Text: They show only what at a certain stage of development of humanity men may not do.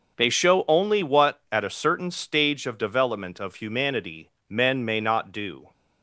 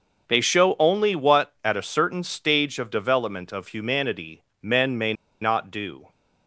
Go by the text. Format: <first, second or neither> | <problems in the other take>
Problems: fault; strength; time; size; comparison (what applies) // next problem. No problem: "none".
first | starts louder than the rest; until 1.3 s; 6 dB; also in the first // pauses between "humanity" and "men"; slight; at 4.4 s; 0.20 s long; slight in the first // pauses between "may" and "not"; slight; at 5.1 s; 0.28 s long